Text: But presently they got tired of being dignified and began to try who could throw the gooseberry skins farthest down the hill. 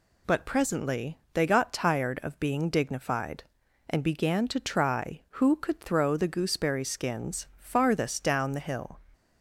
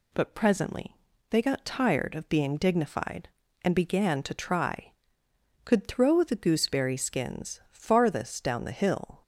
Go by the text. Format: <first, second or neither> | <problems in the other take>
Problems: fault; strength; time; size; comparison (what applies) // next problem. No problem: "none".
first | pauses between "presently" and "they"; slight; at 0.9 s; 0.34 s long; slight in the first // skips "who"; at 5.2 s